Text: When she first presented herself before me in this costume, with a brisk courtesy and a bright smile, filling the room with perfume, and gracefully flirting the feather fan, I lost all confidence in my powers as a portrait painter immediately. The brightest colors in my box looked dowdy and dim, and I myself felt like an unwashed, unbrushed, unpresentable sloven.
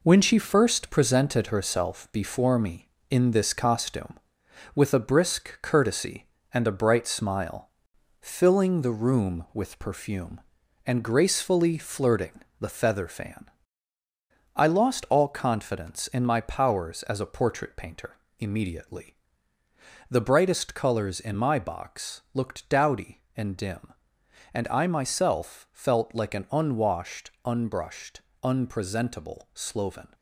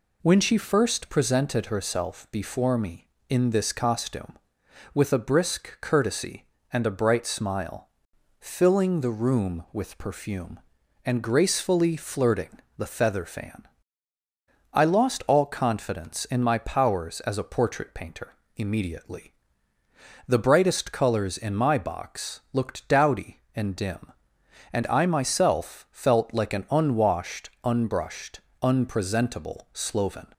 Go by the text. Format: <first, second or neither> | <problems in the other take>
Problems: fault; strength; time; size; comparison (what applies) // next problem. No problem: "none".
second | gets quieter; throughout; 6.5 dB // pauses between "flirting" and "the"; slight; at 12.4 s; 0.18 s long; slight in the second // pauses between "painter" and "immediately"; slight; at 18.1 s; 0.22 s long; slight in the second